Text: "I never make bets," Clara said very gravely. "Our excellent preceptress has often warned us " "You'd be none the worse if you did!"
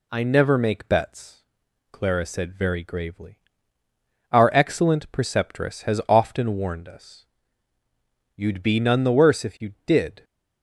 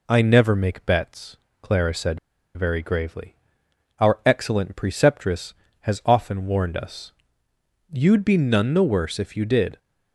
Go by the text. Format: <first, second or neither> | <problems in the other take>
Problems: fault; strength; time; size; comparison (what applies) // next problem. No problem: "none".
first | pauses between "said" and "very"; at 2.1 s; 0.37 s long